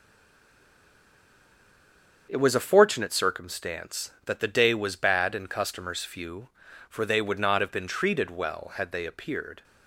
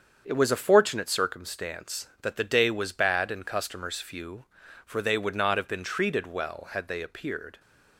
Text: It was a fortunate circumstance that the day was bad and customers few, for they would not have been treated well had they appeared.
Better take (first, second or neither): second